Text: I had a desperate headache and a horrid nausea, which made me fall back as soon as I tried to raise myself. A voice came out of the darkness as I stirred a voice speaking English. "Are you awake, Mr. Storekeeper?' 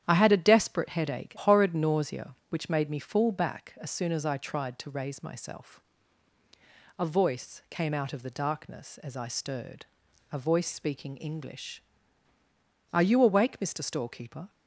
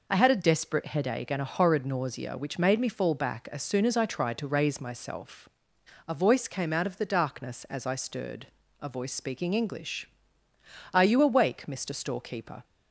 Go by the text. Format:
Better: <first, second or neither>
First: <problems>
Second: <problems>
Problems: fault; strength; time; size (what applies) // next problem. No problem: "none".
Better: second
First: starts louder than the rest; strong; until 1.0 s; 10 dB // skips "and a"; at 1.3 s // pauses between "stirred" and "a"; noticeable; at 9.8 s; 0.46 s long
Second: pauses between "stirred" and "a"; slight; at 8.4 s; 0.34 s long